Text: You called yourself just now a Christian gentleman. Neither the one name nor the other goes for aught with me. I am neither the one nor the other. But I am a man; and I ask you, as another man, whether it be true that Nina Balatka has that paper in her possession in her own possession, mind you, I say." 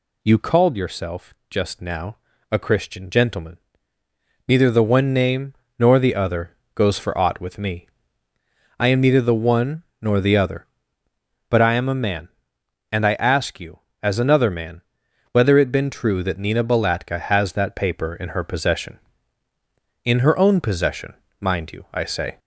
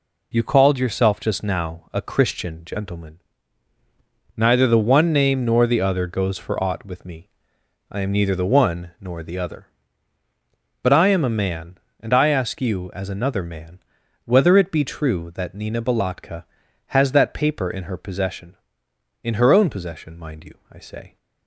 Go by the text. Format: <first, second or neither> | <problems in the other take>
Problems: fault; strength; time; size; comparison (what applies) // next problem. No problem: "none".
second | pauses between "yourself" and "just"; slight; at 1.3 s; 0.16 s long // pauses between "now" and "a"; slight; at 2.1 s; 0.34 s long // pauses between "name" and "nor"; slight; at 5.5 s; 0.24 s long // pauses between "other" and "goes"; slight; at 6.5 s; 0.20 s long // pauses between "one" and "nor"; slight; at 9.8 s; 0.18 s long // says "been" for "be"; at 15.7 s